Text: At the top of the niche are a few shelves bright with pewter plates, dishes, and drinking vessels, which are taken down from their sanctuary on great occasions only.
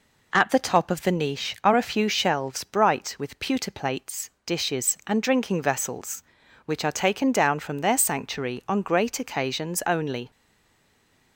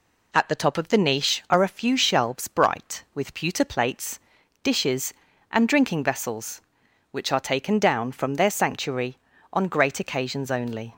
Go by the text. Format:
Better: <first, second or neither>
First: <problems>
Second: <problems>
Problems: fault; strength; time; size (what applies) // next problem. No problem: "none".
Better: second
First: stays silent after the last word; from 10.3 s on; 1.0 s long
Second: none